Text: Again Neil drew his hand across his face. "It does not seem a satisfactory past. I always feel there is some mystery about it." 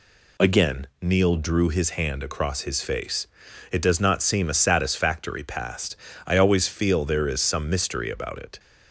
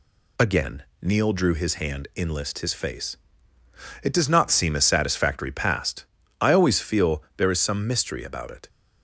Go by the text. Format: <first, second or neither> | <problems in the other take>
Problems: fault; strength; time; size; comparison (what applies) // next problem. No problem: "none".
first | pauses between "Again" and "Neil"; slight; at 0.8 s; 0.18 s long // says "inlist" for "across"; at 2.1 s